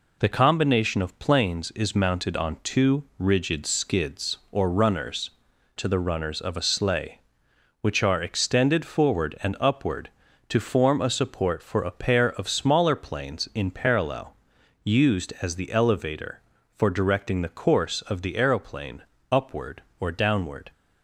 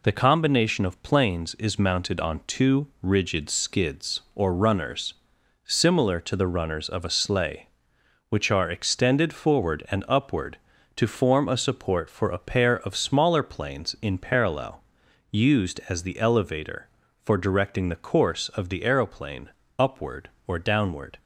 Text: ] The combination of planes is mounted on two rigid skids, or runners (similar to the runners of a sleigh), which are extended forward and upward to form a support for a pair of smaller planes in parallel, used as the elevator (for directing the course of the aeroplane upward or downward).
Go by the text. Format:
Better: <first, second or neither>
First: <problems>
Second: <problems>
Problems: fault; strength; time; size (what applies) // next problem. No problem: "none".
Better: second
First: pauses between "two" and "rigid"; slight; at 3.0 s; 0.16 s long // skips "similar"; at 5.5 s // pauses between "aeroplane" and "upward"; slight; at 19.0 s; 0.26 s long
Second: pauses between "two" and "rigid"; slight; at 2.8 s; 0.16 s long // pauses between "aeroplane" and "upward"; slight; at 19.5 s; 0.26 s long